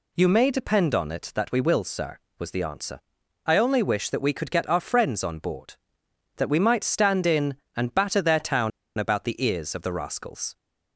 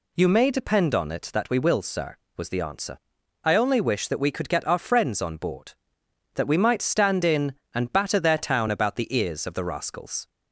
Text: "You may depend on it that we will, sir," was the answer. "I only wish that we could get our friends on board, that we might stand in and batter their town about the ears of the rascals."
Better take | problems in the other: second | pauses between "town" and "about"; slight; at 8.7 s; 0.28 s long

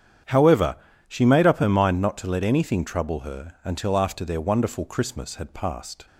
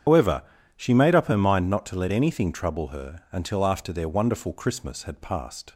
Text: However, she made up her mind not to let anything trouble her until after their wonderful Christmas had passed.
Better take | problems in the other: first | loses the start of "However"; at 0.0 s; 145 ms // starts louder than the rest; strong; until 1.4 s; 8 dB; strong in the first

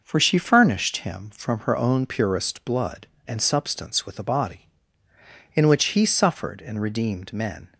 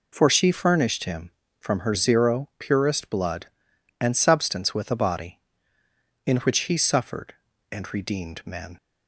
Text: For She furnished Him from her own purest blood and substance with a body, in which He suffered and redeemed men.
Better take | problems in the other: first | says "zero" for "own"; at 1.9 s

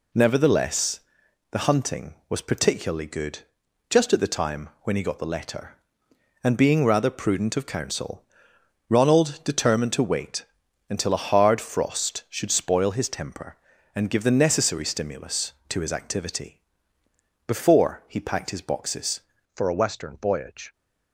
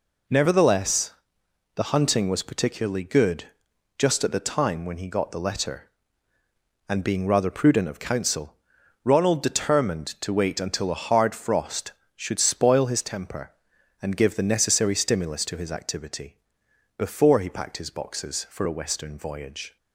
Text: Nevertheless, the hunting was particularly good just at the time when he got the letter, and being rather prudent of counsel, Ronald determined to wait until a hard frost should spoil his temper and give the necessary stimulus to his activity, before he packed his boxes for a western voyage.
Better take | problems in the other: second | pauses between "good" and "just"; noticeable; at 3.4 s; 0.48 s long; noticeable in the second // pauses between "wait" and "until"; at 10.4 s; 0.44 s long // changes voice at "for"; from 19.5 s on; 1.2 s long

